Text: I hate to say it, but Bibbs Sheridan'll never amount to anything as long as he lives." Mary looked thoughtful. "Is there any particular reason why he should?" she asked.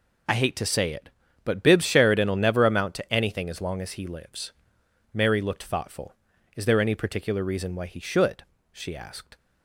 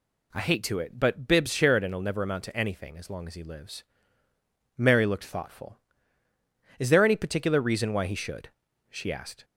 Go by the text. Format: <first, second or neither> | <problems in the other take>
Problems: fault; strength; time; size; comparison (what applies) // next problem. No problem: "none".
first | skips "say"; at 0.7 s